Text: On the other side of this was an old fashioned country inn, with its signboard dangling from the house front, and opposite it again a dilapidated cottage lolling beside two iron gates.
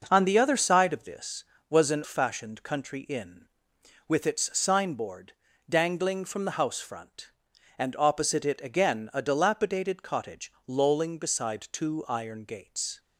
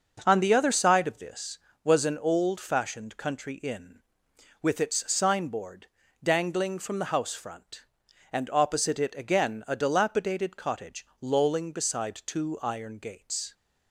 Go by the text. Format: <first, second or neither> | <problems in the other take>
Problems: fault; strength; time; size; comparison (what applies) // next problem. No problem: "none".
second | skips "old"; at 2.0 s // pauses between "signboard" and "dangling"; slight; at 5.3 s; 0.36 s long; slight in the second // pauses between "cottage" and "lolling"; slight; at 10.5 s; 0.16 s long; slight in the second